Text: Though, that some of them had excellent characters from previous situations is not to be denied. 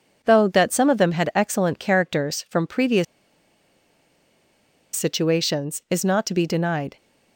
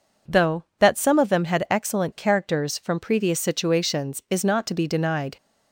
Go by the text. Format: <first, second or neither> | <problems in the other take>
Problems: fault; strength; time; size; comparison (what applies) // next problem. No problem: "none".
second | pauses between "previous" and "situations"; strong; at 3.0 s; 1.9 s long